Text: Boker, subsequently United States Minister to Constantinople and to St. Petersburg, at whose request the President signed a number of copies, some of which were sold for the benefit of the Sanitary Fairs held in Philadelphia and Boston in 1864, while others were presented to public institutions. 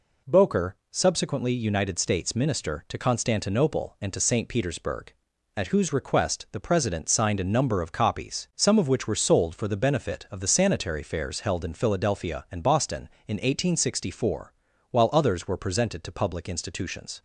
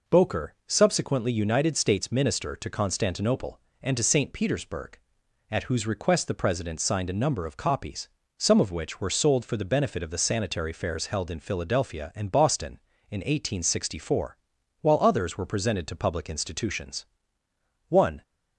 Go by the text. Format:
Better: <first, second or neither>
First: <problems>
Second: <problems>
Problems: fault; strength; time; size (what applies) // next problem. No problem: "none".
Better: first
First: none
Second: goes on to say "One"; slight; from 17.8 s on; 0.34 s long